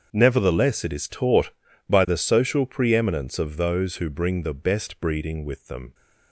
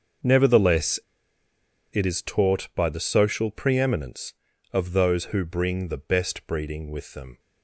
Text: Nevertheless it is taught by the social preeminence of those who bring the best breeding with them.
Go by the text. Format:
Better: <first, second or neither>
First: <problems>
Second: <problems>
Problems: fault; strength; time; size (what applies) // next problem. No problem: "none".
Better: first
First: starts louder than the rest; until 1.1 s; 7 dB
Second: starts louder than the rest; until 2.1 s; 6.5 dB // pauses between "Nevertheless" and "it"; noticeable; at 0.9 s; 0.93 s long